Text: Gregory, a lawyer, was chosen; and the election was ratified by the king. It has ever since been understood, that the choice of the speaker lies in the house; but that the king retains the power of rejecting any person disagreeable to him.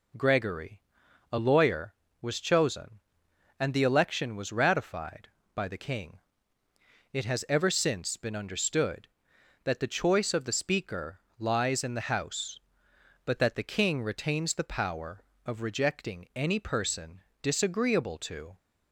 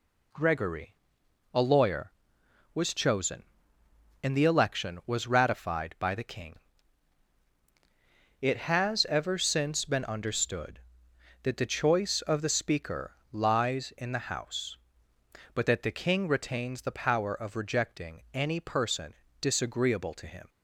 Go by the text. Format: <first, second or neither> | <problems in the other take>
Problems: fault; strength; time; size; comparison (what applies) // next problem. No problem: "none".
second | pauses between "speaker" and "lies"; slight; at 11.1 s; 0.18 s long; slight in the second // pauses between "person" and "disagreeable"; slight; at 17.2 s; 0.22 s long; slight in the second // stops before "him"; at 18.5 s